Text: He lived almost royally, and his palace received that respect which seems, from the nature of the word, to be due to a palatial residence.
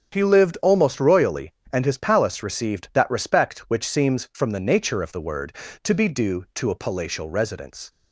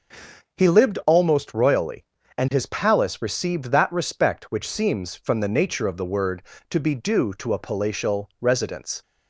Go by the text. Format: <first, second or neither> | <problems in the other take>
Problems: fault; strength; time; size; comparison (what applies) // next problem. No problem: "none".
neither | starts louder than the rest; the same in both